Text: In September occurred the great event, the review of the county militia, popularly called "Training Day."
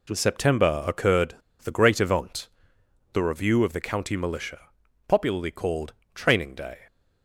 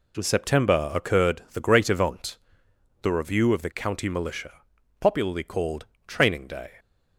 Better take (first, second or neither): second